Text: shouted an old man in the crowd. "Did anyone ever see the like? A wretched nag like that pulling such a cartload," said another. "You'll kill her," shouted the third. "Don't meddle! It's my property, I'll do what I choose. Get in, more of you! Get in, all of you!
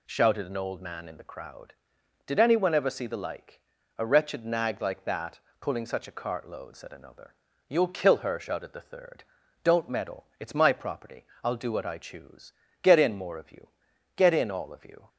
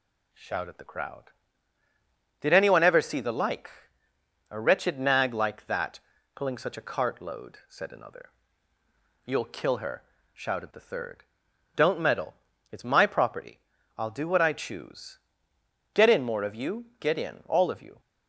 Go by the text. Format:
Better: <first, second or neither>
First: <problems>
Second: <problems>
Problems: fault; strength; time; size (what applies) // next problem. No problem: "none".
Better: first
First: pauses between "that" and "pulling"; slight; at 5.4 s; 0.18 s long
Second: skips "an old man in"; at 0.7 s // pauses between "that" and "pulling"; slight; at 5.9 s; 0.36 s long